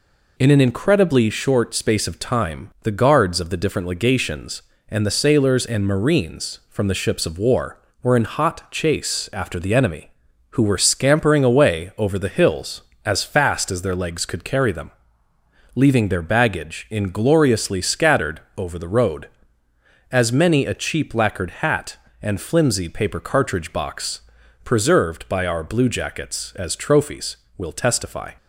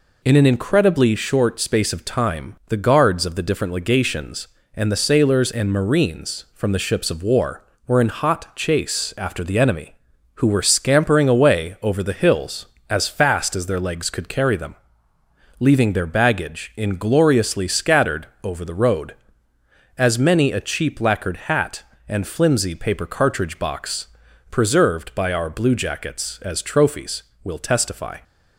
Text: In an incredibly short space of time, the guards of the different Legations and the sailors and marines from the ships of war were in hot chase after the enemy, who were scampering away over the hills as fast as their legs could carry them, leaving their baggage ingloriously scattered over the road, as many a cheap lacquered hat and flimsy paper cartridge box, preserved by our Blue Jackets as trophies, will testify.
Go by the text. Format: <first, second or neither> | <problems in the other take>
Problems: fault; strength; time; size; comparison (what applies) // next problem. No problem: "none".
neither | pauses between "scattered" and "over"; slight; the same in both